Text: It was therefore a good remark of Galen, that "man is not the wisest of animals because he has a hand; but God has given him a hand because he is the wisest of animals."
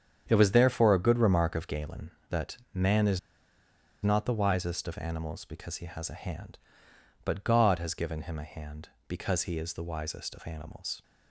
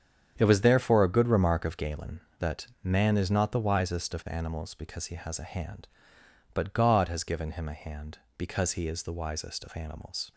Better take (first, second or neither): second